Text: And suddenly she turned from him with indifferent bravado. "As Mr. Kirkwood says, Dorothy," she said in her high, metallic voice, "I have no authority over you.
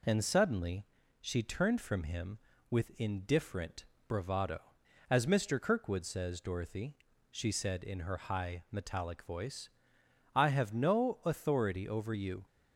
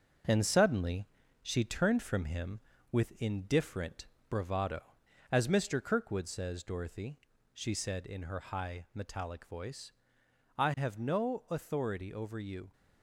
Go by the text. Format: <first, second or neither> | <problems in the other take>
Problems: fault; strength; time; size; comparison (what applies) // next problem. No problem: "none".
first | gets quieter; noticeable; throughout; 5 dB // pauses between "suddenly" and "she"; slight; at 1.0 s; 0.36 s long; slight in the first // pauses between "indifferent" and "bravado"; slight; at 4.0 s; 0.20 s long; slight in the first